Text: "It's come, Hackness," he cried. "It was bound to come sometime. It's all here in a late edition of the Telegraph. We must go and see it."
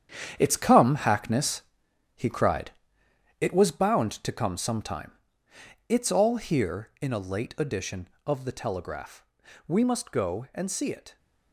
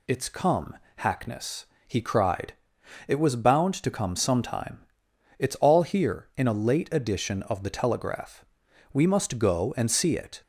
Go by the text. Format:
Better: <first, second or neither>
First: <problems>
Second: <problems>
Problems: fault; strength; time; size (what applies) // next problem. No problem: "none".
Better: second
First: gets quieter; strong; throughout; 10 dB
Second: none